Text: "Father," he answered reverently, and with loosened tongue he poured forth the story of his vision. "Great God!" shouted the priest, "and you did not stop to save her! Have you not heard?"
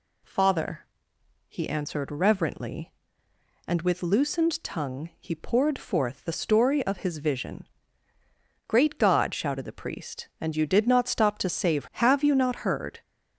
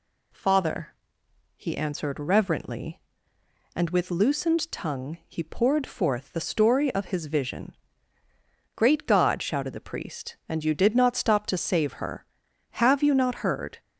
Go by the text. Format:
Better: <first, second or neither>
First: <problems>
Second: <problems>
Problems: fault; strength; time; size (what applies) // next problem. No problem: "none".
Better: second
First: skips "her"; at 11.9 s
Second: none